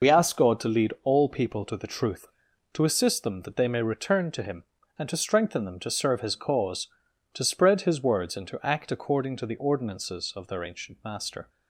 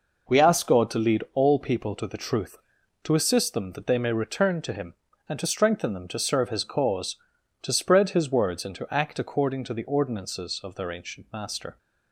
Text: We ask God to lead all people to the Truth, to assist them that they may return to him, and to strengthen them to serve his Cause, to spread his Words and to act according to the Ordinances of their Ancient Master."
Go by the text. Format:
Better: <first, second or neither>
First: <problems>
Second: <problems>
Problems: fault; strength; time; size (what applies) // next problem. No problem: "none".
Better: second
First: loses the start of "We"; at 0.0 s; 40 ms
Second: none